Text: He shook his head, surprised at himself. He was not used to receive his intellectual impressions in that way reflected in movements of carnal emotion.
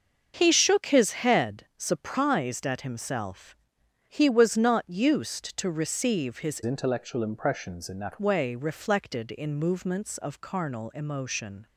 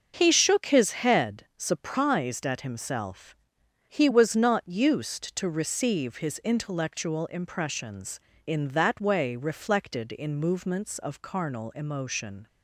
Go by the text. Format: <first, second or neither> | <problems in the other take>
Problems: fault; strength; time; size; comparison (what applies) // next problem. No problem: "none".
second | starts louder than the rest; until 1.3 s; 6.5 dB; also in the second // changes voice from "intellectual" to "that"; from 6.6 to 8.2 s; 1.6 s long